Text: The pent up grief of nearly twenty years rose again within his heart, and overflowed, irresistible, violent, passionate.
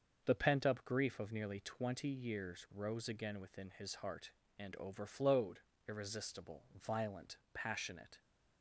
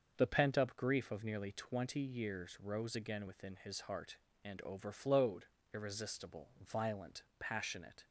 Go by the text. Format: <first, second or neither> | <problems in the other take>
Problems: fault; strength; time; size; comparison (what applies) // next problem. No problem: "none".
neither | starts louder than the rest; the same in both